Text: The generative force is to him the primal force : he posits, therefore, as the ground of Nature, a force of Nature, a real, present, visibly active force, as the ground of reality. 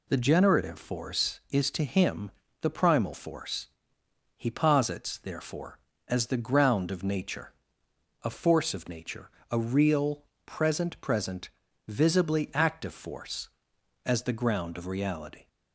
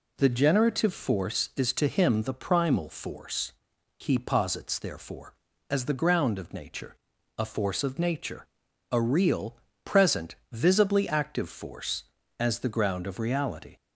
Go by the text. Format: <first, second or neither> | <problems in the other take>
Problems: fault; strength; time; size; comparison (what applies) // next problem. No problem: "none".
second | pauses between "him" and "the"; slight; at 2.3 s; 0.32 s long // says "present" twice; at 11.0 s